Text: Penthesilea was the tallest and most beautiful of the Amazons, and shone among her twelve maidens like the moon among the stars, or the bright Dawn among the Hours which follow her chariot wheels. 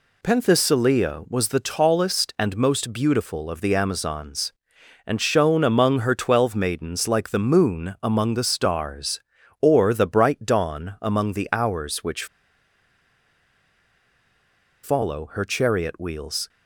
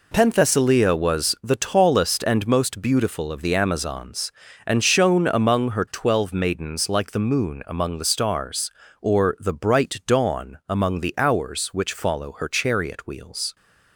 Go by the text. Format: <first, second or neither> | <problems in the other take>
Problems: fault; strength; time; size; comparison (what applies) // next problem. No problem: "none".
second | pauses between "which" and "follow"; strong; at 12.2 s; 2.5 s long